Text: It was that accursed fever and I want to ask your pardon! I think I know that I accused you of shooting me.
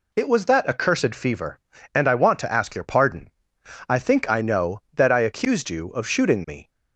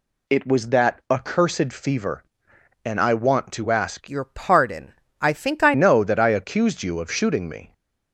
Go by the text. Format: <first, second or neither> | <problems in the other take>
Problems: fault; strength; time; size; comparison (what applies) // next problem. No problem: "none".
first | changes voice from "your" to "I"; from 4.0 to 5.7 s; 1.7 s long